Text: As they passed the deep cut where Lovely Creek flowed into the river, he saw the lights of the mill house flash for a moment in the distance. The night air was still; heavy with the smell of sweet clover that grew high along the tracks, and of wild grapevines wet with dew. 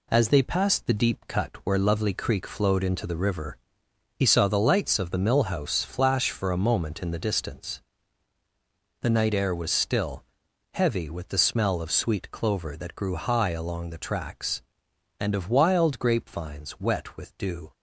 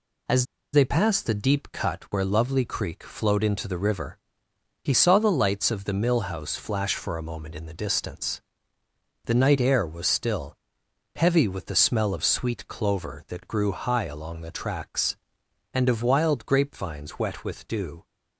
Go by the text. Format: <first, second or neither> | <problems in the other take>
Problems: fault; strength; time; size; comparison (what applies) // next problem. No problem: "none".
first | pauses between "As" and "they"; slight; at 0.4 s; 0.28 s long